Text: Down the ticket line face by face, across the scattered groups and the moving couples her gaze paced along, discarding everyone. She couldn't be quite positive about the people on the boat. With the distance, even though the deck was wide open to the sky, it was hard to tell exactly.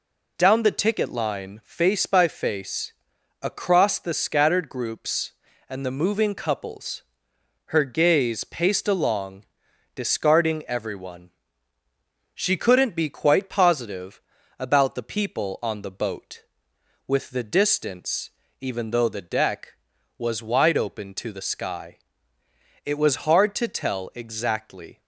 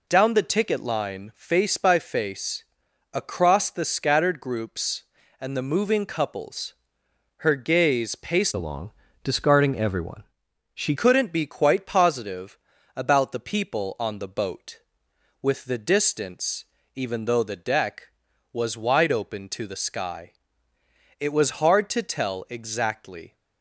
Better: first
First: pauses between "couples" and "her"; noticeable; at 7.0 s; 0.68 s long // pauses between "positive" and "about"; at 14.1 s; 0.38 s long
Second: pauses between "couples" and "her"; noticeable; at 6.7 s; 0.68 s long // changes voice from "along" to "She"; from 8.5 to 10.9 s; 2.4 s long // pauses between "positive" and "about"; at 12.5 s; 0.38 s long

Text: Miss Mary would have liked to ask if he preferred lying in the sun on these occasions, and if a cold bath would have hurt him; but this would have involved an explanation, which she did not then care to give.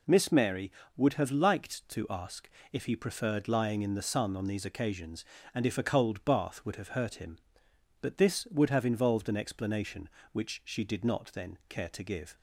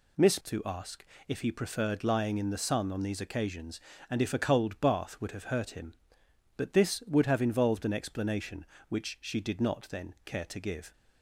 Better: first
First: pauses between "ask" and "if"; slight; at 2.4 s; 0.26 s long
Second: skips "Mary would have liked"; at 0.4 s // pauses between "ask" and "if"; slight; at 1.0 s; 0.26 s long

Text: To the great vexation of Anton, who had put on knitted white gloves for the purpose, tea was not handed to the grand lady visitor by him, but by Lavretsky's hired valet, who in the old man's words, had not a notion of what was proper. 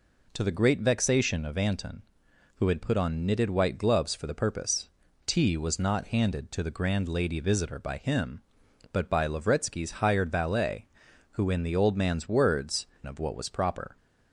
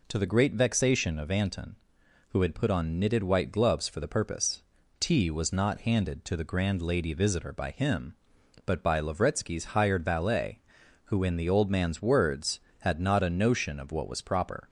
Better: second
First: skips "had not a notion"; at 12.9 s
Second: none

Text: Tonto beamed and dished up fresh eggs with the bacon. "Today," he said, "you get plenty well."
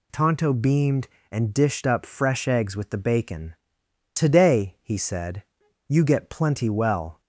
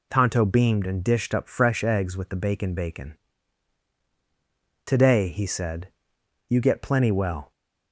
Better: first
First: none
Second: says "bacon" twice; at 2.7 s

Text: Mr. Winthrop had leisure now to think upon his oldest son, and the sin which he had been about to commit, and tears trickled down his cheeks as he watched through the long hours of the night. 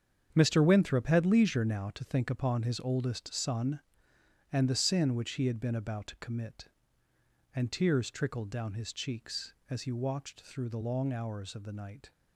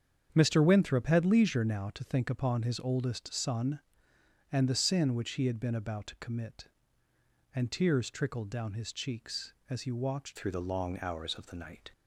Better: first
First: starts louder than the rest; strong; until 1.3 s; 7.5 dB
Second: starts louder than the rest; strong; until 1.3 s; 7.5 dB // changes voice at "through"; from 10.3 s on; 1.6 s long

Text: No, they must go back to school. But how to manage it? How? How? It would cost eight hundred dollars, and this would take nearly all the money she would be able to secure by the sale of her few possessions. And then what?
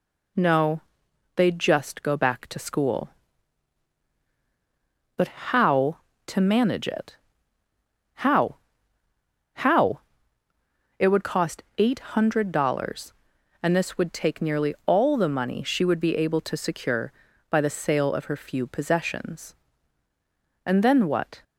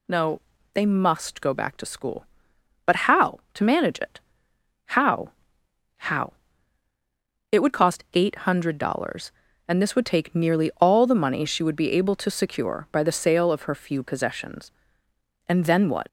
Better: second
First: says "just" for "must"; at 1.5 s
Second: none

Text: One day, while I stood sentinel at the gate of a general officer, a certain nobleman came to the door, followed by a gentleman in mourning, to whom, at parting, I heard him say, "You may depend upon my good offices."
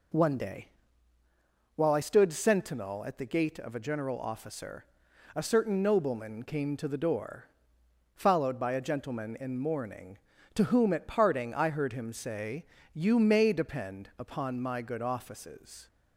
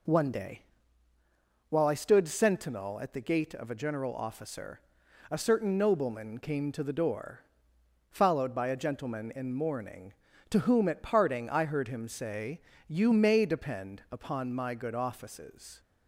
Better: neither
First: none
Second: none

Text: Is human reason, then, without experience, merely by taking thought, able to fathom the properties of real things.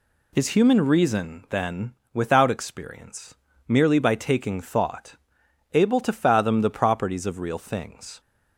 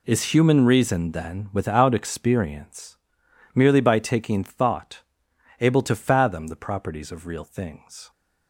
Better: neither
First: none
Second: none

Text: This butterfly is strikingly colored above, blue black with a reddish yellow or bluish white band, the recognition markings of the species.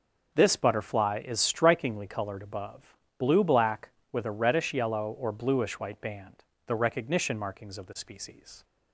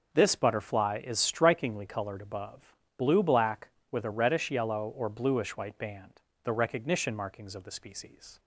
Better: neither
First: none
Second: none

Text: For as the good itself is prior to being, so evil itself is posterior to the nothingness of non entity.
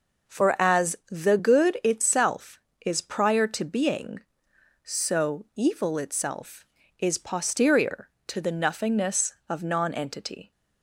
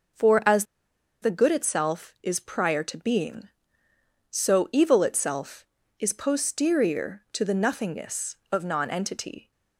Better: first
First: none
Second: pauses between "as" and "the"; noticeable; at 0.6 s; 0.57 s long

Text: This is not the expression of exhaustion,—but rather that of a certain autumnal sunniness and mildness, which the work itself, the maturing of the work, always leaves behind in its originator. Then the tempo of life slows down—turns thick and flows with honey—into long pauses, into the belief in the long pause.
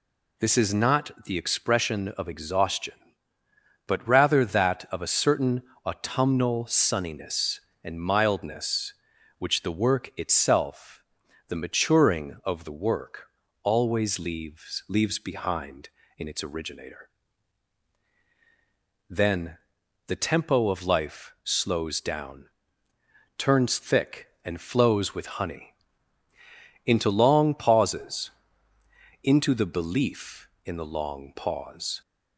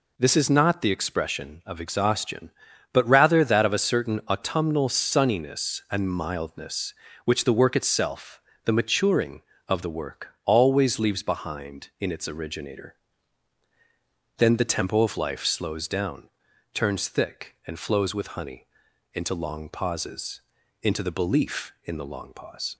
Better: second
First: pauses between "certain" and "autumnal"; slight; at 5.6 s; 0.22 s long // says "leaves" twice; at 14.8 s // pauses between "Then" and "the"; noticeable; at 19.5 s; 0.48 s long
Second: none

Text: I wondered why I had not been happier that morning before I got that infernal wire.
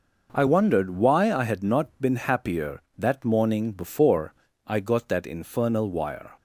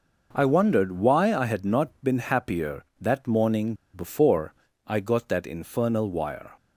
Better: first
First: pauses between "before" and "I"; slight; at 4.3 s; 0.32 s long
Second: pauses between "morning" and "before"; slight; at 3.7 s; 0.20 s long // pauses between "before" and "I"; slight; at 4.5 s; 0.32 s long

